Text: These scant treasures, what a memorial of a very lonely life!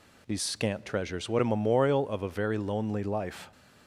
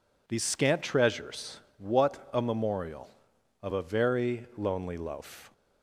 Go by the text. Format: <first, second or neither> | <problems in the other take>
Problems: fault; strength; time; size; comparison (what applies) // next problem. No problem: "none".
first | says "loaf" for "life"; at 4.9 s